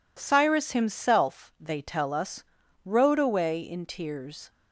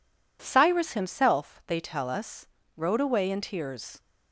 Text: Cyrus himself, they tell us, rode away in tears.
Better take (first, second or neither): neither